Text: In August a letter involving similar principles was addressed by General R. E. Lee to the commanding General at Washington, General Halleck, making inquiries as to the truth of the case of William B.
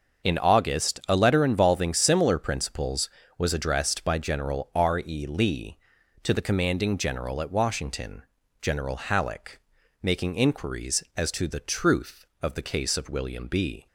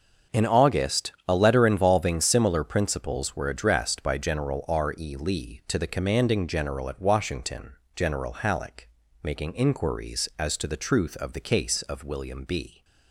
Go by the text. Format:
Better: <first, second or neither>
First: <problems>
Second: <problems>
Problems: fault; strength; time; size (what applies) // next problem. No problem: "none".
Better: first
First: starts louder than the rest; until 1.3 s; 6.5 dB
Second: starts louder than the rest; noticeable; until 1.4 s; 6 dB // says "were" for "was"; at 3.3 s